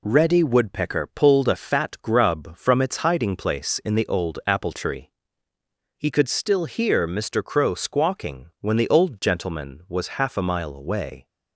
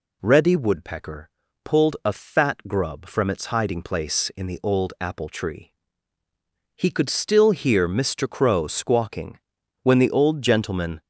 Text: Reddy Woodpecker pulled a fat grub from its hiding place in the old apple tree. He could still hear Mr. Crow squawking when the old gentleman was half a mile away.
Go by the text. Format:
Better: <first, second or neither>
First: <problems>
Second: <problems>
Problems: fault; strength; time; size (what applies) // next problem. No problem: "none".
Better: first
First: none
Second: pauses between "Woodpecker" and "pulled"; slight; at 1.2 s; 0.36 s long // pauses between "squawking" and "when"; noticeable; at 9.3 s; 0.46 s long // stops before "was half a mile away"; at 11.0 s